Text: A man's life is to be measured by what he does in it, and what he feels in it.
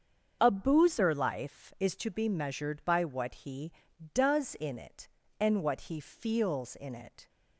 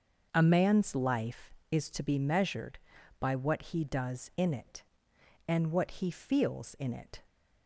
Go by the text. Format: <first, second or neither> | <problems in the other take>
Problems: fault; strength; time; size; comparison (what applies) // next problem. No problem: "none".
second | starts louder than the rest; until 1.4 s; 6.5 dB; also in the second // says "boozer" for "man's"; at 0.4 s